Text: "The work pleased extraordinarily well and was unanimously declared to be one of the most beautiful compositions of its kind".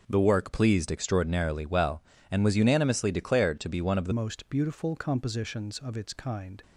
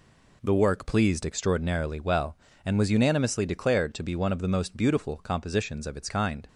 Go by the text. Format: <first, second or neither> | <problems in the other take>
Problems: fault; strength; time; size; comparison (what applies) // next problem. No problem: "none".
second | changes voice at "most"; from 4.1 s on; 2.5 s long